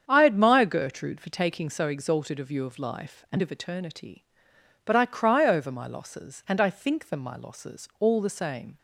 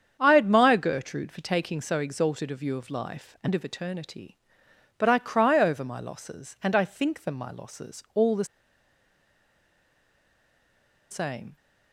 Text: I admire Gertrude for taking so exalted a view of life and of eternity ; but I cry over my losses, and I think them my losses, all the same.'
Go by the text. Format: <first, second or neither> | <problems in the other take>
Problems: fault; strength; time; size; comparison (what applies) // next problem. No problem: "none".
first | starts louder than the rest; strong; until 1.2 s; 8 dB; strong in the first // pauses between "the" and "same"; strong; at 8.4 s; 2.6 s long